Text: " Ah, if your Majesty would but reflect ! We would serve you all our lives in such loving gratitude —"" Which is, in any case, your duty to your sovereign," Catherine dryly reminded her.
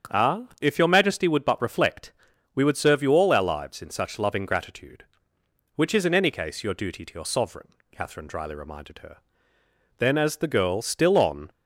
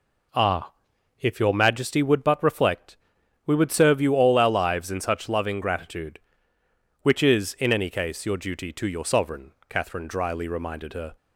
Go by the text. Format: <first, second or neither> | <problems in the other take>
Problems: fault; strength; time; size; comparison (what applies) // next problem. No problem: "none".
second | starts louder than the rest; strong; until 1.3 s; 7.5 dB // goes on to say "Then as the girl still on"; from 9.9 s on; 1.5 s long